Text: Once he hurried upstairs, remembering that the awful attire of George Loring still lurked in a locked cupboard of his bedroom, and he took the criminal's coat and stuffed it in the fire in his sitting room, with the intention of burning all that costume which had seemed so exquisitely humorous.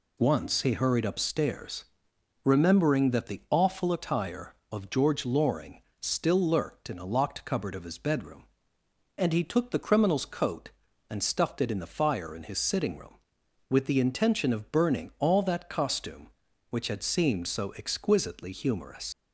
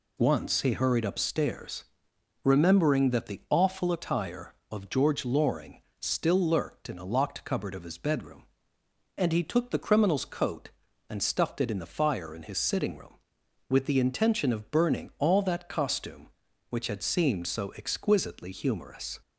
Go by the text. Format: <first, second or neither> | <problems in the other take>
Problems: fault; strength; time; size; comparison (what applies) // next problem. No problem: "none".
second | pauses between "Loring" and "still"; slight; at 5.8 s; 0.20 s long; slight in the second // leaves "humorous" unfinished; at 19.1 s; 90 ms